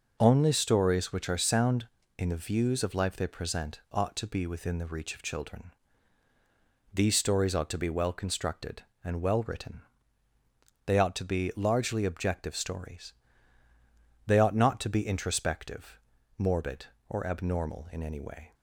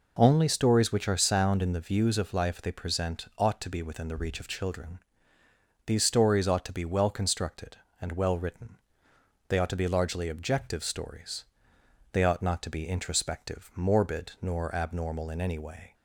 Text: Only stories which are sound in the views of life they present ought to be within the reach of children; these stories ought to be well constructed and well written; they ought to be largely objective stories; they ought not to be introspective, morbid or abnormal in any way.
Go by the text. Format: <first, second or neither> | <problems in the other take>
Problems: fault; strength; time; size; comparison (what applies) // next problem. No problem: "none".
first | says "nor" for "or"; at 14.4 s